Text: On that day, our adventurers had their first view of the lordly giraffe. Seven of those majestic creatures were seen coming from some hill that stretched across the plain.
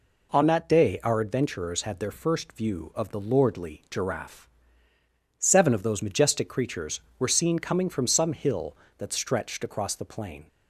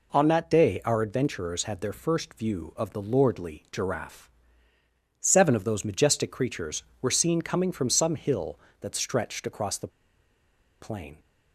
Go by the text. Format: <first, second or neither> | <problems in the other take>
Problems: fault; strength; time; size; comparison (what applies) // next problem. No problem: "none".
first | pauses between "the" and "plain"; noticeable; at 9.8 s; 0.92 s long